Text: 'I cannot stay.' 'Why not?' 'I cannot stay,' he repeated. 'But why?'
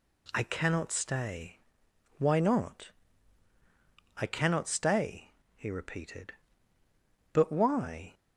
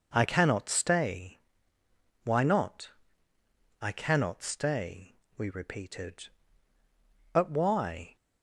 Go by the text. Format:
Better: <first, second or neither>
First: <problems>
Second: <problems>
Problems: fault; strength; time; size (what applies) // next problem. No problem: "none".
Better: first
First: none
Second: says "we" for "he"; at 5.3 s